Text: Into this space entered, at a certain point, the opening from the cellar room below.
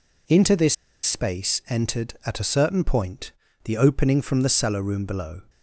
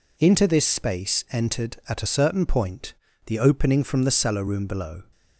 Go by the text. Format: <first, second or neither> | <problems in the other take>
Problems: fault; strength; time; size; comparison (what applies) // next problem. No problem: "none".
second | pauses between "this" and "space"; slight; at 0.7 s; 0.28 s long